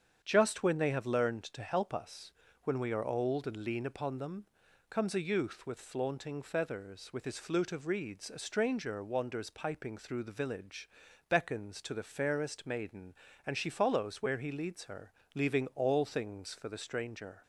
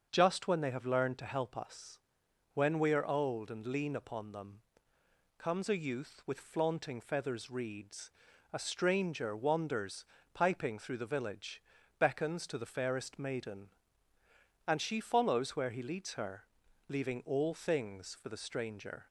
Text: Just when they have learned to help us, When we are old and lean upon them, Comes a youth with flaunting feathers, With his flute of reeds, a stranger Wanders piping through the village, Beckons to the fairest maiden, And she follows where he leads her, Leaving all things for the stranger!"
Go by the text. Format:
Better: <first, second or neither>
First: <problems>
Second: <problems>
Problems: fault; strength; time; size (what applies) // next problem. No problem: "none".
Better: first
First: starts louder than the rest; strong; until 1.2 s; 8 dB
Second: starts louder than the rest; until 1.1 s; 6.5 dB // skips "With his flute of"; at 7.5 s // pauses between "Wanders" and "piping"; slight; at 10.0 s; 0.28 s long